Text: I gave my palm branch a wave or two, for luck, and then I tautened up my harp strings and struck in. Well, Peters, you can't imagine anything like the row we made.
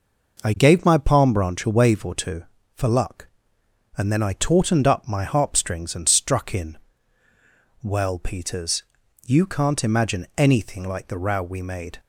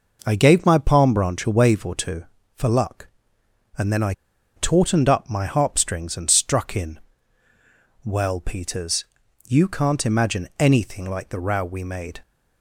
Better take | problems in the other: first | pauses between "I" and "tautened"; at 4.1 s; 0.43 s long

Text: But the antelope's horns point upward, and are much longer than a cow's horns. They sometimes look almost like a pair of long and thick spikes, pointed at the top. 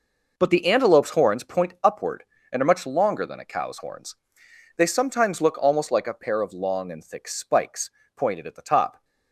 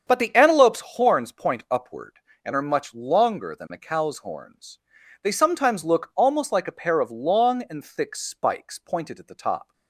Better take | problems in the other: first | starts louder than the rest; strong; until 1.1 s; 7 dB

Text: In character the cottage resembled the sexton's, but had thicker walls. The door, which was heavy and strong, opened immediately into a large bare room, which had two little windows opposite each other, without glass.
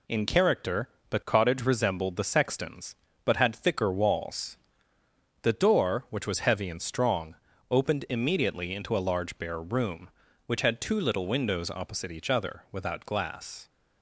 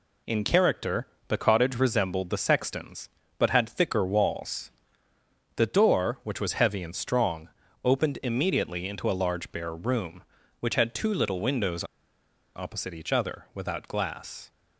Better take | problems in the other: first | pauses between "character" and "the"; slight; at 1.0 s; 0.22 s long; slight in the first // pauses between "windows" and "opposite"; noticeable; at 11.8 s; 0.71 s long

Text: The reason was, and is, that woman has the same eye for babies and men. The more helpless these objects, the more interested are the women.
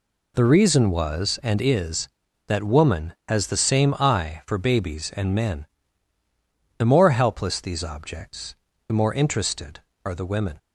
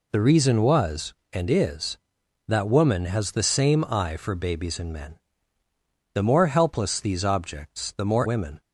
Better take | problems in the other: first | skips "interested are the"; at 8.2 s

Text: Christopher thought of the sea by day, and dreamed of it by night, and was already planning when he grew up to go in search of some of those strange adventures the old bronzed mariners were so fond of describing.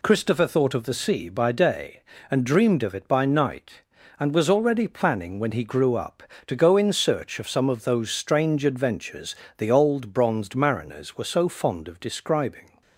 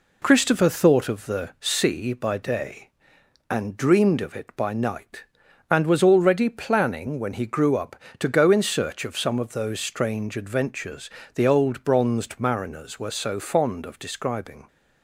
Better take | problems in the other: neither | pauses between "adventures" and "the"; slight; the same in both

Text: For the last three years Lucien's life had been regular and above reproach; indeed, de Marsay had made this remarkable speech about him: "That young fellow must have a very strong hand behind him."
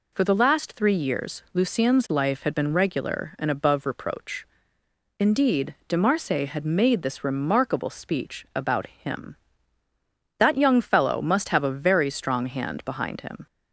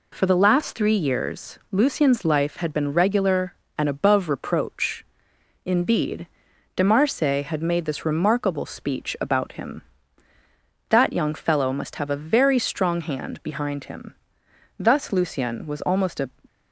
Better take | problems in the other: first | goes on to say "Thus Lucien was almost a"; from 14.7 s on; 1.5 s long

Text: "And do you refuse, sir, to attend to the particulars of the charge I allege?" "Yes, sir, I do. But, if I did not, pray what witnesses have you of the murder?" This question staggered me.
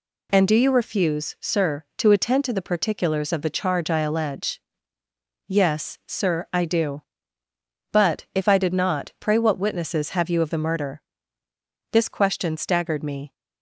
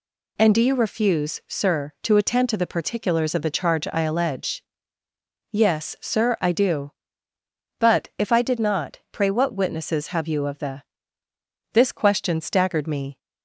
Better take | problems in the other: first | skips "murder"; at 11.2 s

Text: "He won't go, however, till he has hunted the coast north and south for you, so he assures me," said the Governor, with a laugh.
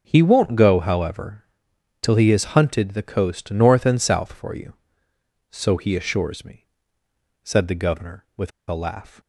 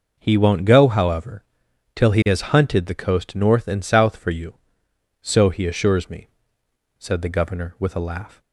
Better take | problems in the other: second | starts louder than the rest; noticeable; until 1.0 s; 6 dB // pauses between "with" and "a"; slight; at 8.5 s; 0.19 s long

